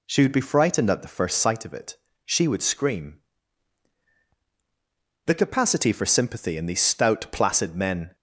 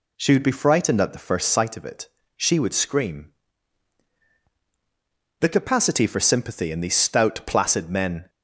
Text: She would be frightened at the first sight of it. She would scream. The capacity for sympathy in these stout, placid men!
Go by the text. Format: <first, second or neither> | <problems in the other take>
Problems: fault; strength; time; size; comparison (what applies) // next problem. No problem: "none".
neither | none